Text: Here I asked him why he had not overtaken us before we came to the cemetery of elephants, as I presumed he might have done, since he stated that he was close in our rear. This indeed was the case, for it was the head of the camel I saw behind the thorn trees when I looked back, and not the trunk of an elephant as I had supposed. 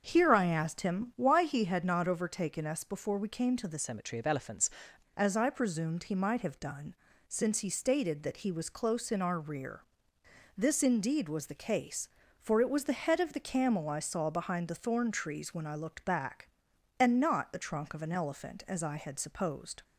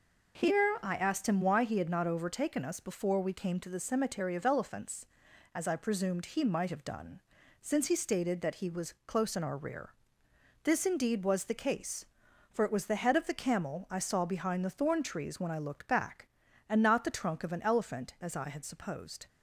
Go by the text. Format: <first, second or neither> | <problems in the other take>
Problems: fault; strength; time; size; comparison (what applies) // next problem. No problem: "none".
second | starts louder than the rest; until 1.0 s; 6.5 dB // changes voice from "cemetery" to "elephants"; from 3.7 to 4.7 s; 1.0 s long